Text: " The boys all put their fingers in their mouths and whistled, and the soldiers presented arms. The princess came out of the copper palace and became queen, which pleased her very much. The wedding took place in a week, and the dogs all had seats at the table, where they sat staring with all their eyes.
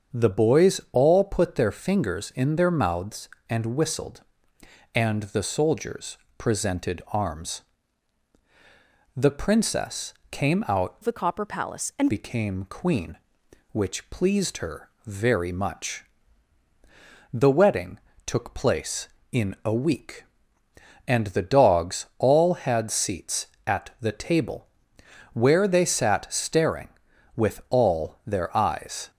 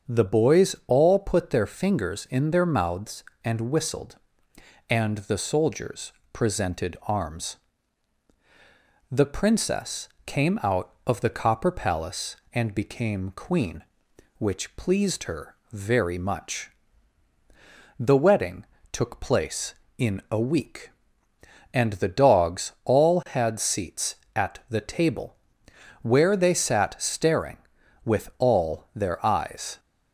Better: second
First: starts louder than the rest; strong; until 1.2 s; 7 dB // pauses between "soldiers" and "presented"; slight; at 6.1 s; 0.20 s long // pauses between "princess" and "came"; slight; at 10.1 s; 0.18 s long // changes voice from "of" to "and"; from 11.0 to 12.1 s; 1.1 s long // pauses between "her" and "very"; slight; at 14.9 s; 0.16 s long // pauses between "wedding" and "took"; slight; at 17.9 s; 0.28 s long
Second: starts louder than the rest; strong; until 1.1 s; 7 dB // pauses between "soldiers" and "presented"; slight; at 6.1 s; 0.20 s long // pauses between "princess" and "came"; slight; at 10.0 s; 0.18 s long // pauses between "her" and "very"; slight; at 15.5 s; 0.16 s long // pauses between "wedding" and "took"; slight; at 18.6 s; 0.28 s long

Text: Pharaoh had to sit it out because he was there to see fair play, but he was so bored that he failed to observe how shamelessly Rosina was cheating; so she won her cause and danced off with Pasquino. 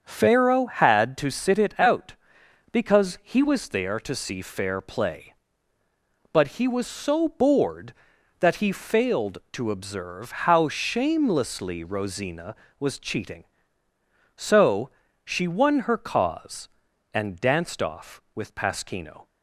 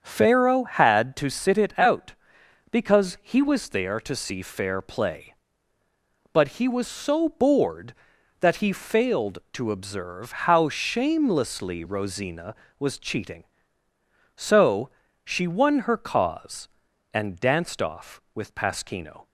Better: neither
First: starts louder than the rest; until 1.0 s; 7 dB // pauses between "so" and "she"; slight; at 14.8 s; 0.34 s long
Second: starts louder than the rest; until 1.0 s; 7 dB // pauses between "so" and "she"; slight; at 14.8 s; 0.34 s long

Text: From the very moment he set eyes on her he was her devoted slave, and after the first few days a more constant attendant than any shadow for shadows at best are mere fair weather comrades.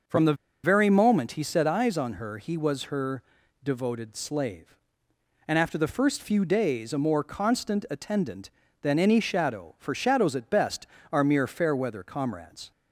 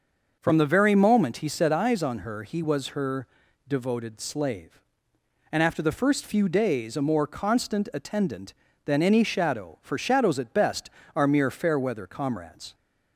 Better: second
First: starts louder than the rest; until 1.3 s; 6 dB // pauses between "the" and "very"; slight; at 0.3 s; 0.30 s long // pauses between "her" and "devoted"; at 3.2 s; 0.40 s long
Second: starts louder than the rest; until 1.4 s; 6 dB // pauses between "her" and "devoted"; at 3.2 s; 0.40 s long

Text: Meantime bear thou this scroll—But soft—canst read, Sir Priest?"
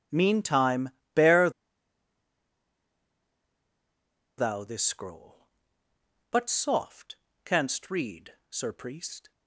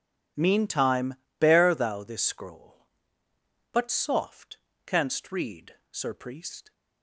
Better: second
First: pauses between "Meantime" and "bear"; slight; at 0.8 s; 0.24 s long // pauses between "bear" and "thou"; strong; at 1.4 s; 2.8 s long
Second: pauses between "Meantime" and "bear"; slight; at 1.1 s; 0.24 s long

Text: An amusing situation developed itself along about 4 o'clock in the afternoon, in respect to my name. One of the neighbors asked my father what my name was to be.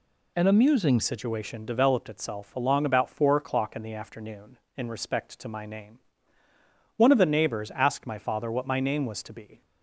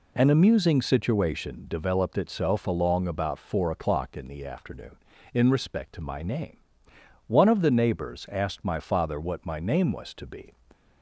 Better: second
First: changes voice at "situation"; from 1.0 s on; 8.6 s long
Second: none

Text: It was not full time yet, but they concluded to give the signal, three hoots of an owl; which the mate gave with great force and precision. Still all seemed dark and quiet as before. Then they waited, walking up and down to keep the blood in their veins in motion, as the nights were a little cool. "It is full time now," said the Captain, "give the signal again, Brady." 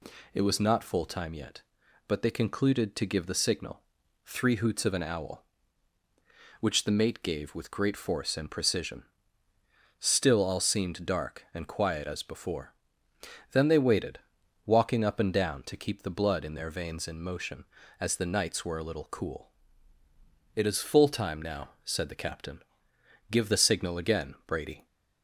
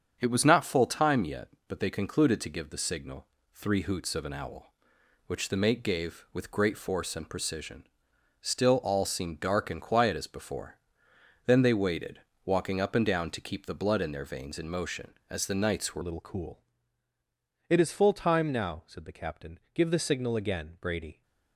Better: first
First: none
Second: starts louder than the rest; strong; until 1.2 s; 7.5 dB // changes voice at "a"; from 16.0 s on; 5.2 s long

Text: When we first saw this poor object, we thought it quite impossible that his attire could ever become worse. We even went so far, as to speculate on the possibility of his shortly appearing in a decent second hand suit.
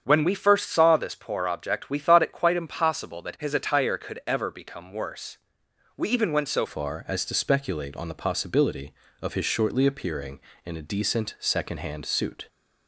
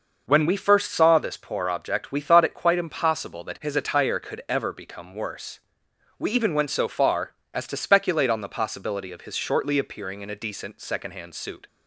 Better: second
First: starts louder than the rest; strong; until 1.0 s; 8 dB // changes voice at "far"; from 6.6 s on; 5.8 s long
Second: none

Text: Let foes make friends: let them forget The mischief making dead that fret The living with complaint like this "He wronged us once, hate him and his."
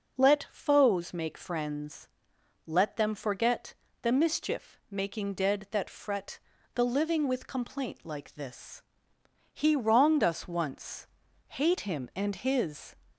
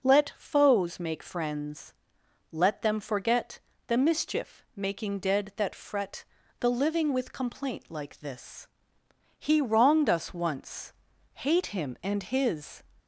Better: neither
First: pauses between "forget" and "The"; slight; at 3.7 s; 0.26 s long // pauses between "fret" and "The"; slight; at 6.3 s; 0.36 s long // pauses between "this" and "He"; noticeable; at 8.7 s; 0.72 s long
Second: pauses between "forget" and "The"; slight; at 3.5 s; 0.26 s long // pauses between "fret" and "The"; slight; at 6.2 s; 0.36 s long // pauses between "this" and "He"; noticeable; at 8.6 s; 0.72 s long

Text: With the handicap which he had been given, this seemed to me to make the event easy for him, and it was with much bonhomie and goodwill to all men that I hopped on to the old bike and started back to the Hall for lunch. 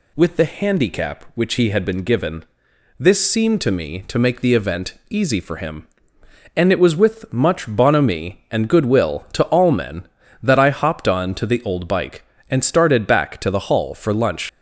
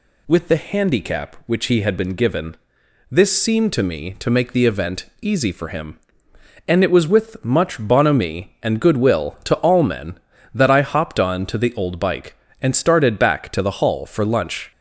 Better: second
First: pauses between "event" and "easy"; slight; at 4.9 s; 0.16 s long // leaves "lunch" unfinished; at 14.4 s; 100 ms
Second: pauses between "event" and "easy"; slight; at 5.0 s; 0.16 s long

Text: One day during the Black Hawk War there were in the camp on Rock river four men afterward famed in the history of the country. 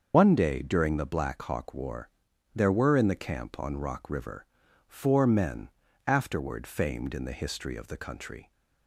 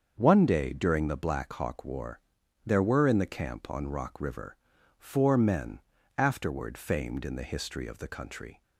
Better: second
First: loses the start of "One"; at 0.1 s; 75 ms // starts louder than the rest; until 1.1 s; 6.5 dB // pauses between "War" and "there"; at 2.0 s; 0.44 s long // pauses between "river" and "four"; at 4.4 s; 0.42 s long // pauses between "men" and "afterward"; slight; at 5.6 s; 0.36 s long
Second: starts louder than the rest; until 1.1 s; 7 dB // pauses between "War" and "there"; at 2.1 s; 0.44 s long // pauses between "river" and "four"; at 4.5 s; 0.42 s long // pauses between "men" and "afterward"; slight; at 5.7 s; 0.36 s long

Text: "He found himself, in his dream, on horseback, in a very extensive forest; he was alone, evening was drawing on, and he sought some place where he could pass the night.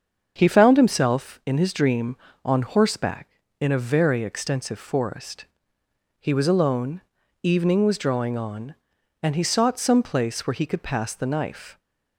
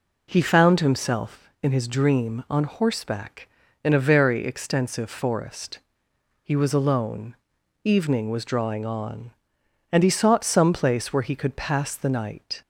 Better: second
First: starts louder than the rest; until 1.3 s; 7 dB // says "knife" for "night"; at 11.2 s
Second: none

